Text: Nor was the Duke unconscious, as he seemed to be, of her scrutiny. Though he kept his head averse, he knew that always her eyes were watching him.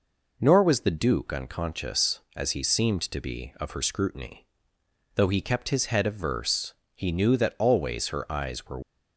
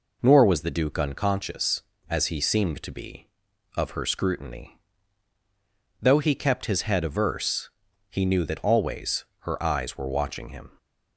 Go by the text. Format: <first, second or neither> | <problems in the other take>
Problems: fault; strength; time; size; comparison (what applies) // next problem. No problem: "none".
second | stops before "watching him"; at 8.8 s